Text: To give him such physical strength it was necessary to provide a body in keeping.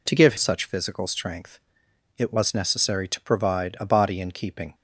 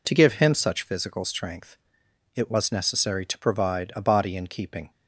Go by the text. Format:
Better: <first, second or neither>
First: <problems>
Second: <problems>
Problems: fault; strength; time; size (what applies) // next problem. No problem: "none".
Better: second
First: skips "him"; at 0.3 s // pauses between "strength" and "it"; noticeable; at 1.5 s; 0.60 s long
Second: pauses between "strength" and "it"; noticeable; at 1.7 s; 0.60 s long